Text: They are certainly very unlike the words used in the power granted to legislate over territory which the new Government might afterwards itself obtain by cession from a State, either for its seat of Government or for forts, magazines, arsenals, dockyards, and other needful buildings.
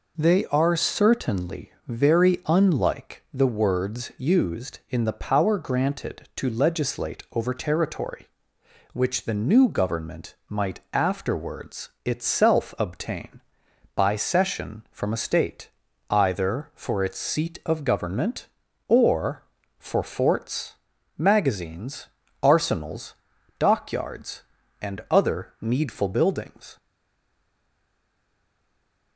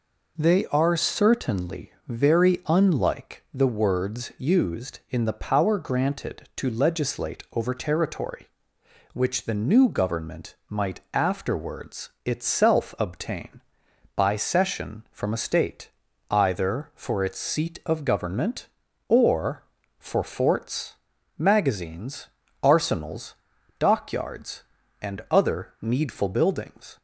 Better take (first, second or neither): second